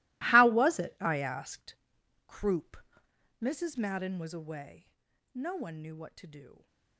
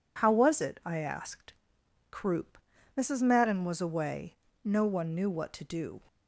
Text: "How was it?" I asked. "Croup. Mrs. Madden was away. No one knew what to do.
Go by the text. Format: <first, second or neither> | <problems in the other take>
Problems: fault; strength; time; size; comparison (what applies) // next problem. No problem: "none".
second | gets quieter; strong; throughout; 18.5 dB